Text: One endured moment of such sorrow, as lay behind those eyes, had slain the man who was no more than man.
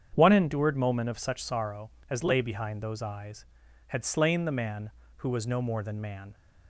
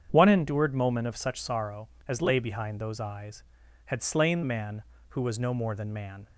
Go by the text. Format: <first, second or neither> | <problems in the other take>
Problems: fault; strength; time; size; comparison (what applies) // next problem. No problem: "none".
first | starts louder than the rest; strong; until 1.1 s; 8 dB; strong in the first // skips "the"; at 4.4 s